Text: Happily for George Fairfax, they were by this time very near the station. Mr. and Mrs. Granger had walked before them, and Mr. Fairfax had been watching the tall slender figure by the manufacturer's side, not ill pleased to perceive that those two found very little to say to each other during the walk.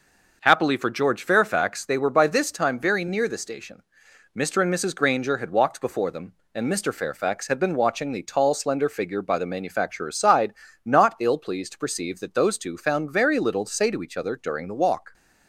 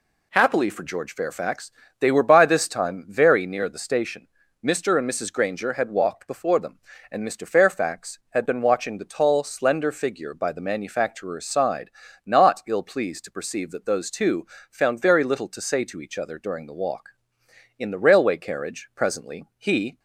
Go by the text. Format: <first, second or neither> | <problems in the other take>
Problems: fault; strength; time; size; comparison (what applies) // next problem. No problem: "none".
first | pauses between "two" and "found"; slight; at 14.4 s; 0.24 s long // goes on to say "In the railway carriage presently he"; strong; from 17.7 s on; 2.2 s long